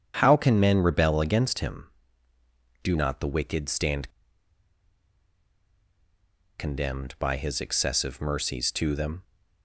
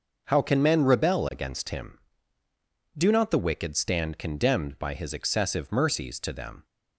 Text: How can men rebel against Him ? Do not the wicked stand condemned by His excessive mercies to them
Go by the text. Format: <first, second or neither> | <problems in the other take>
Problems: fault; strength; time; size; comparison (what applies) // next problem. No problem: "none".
second | starts louder than the rest; strong; until 1.2 s; 8 dB; noticeable in the second // pauses between "stand" and "condemned"; strong; at 4.0 s; 2.4 s long